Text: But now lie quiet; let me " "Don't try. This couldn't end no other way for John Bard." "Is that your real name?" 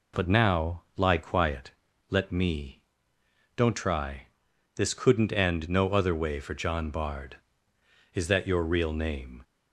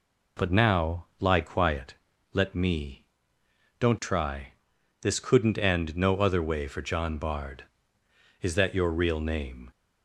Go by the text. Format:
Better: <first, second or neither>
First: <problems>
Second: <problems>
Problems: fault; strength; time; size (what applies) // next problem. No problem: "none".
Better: neither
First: none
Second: none